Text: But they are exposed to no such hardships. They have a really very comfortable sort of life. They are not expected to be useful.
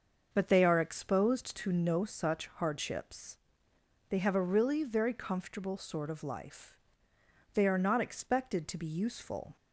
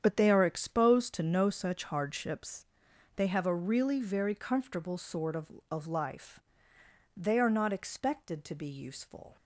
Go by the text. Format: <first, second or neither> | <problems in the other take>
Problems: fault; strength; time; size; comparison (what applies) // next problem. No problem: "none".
first | starts louder than the rest; strong; until 1.0 s; 8.5 dB; also in the first // says "of" twice; at 5.6 s